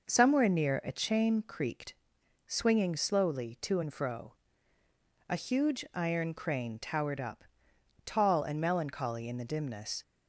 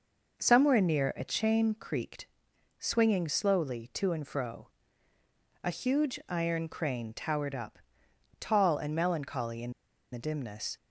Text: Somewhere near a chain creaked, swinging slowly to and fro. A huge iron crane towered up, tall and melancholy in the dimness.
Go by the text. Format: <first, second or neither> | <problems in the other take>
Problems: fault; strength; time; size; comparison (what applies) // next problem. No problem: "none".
first | pauses between "in" and "the"; at 9.7 s; 0.41 s long